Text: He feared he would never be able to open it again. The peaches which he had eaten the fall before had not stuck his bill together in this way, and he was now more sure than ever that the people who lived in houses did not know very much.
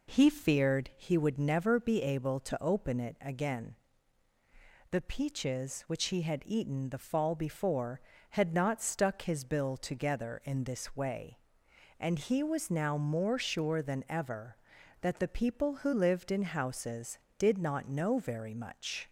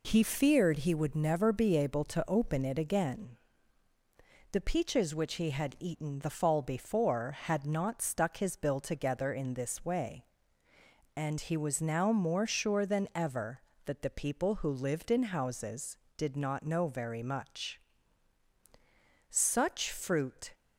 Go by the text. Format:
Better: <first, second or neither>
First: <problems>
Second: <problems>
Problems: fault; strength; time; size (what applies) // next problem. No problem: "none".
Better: first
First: none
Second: goes on to say "Such fruit"; noticeable; from 19.2 s on; 1.2 s long